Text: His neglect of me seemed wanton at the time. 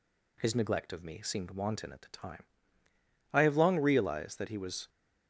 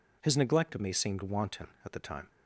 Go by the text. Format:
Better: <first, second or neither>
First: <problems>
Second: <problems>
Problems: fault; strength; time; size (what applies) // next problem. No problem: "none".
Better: second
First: goes on to say "I have long realized that he was"; from 3.3 s on; 1.5 s long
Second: none